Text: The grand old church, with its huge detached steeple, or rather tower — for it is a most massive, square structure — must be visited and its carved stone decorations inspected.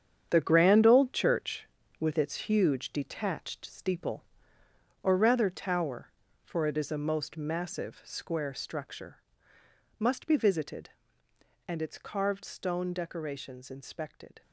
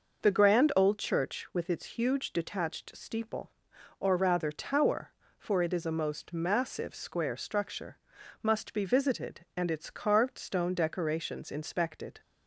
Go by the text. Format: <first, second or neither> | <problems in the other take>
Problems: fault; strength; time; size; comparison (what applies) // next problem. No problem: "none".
second | gets quieter; strong; throughout; 10.5 dB